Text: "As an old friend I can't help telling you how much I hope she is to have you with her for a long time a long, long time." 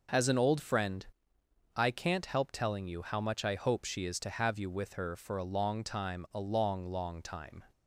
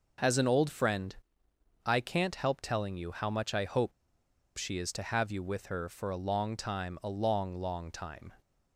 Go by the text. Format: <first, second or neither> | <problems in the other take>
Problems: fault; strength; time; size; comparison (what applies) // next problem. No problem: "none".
first | pauses between "friend" and "I"; noticeable; at 1.1 s; 0.70 s long; noticeable in the first // pauses between "hope" and "she"; noticeable; at 3.9 s; 0.64 s long